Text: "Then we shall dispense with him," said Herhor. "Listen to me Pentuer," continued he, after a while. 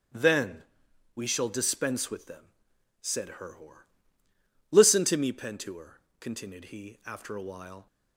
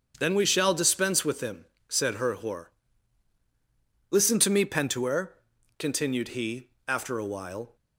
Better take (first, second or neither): second